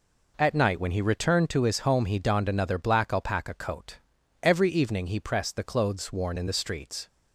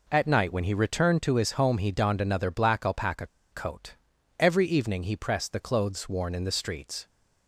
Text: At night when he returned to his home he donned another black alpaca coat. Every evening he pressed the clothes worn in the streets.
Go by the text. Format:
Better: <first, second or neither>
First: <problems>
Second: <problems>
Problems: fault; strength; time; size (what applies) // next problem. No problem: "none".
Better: first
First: none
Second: pauses between "alpaca" and "coat"; slight; at 3.2 s; 0.26 s long